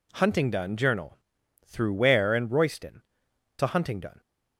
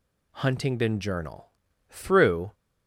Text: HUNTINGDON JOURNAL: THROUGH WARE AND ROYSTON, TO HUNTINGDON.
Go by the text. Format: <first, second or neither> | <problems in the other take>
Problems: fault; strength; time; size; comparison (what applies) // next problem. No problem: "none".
first | stops before "WARE AND ROYSTON TO HUNTINGDON"; at 2.5 s